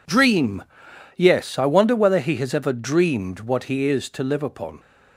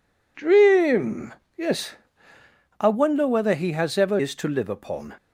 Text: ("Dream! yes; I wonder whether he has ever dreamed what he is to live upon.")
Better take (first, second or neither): first